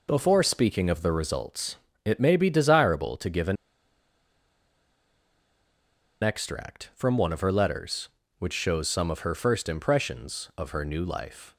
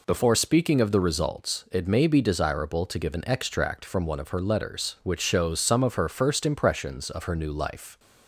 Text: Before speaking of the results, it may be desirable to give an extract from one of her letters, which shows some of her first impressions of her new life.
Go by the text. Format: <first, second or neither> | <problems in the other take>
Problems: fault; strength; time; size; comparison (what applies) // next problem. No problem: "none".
second | pauses between "an" and "extract"; strong; at 3.5 s; 2.6 s long